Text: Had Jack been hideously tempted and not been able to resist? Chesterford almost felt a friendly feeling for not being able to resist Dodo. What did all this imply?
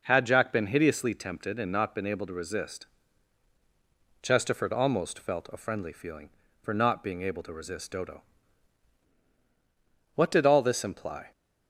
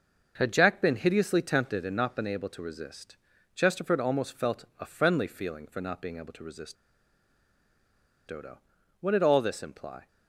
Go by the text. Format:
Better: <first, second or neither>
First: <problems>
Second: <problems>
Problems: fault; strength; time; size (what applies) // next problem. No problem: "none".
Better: first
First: none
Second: starts louder than the rest; noticeable; until 1.3 s; 6 dB // pauses between "resist" and "Dodo"; strong; at 6.7 s; 1.5 s long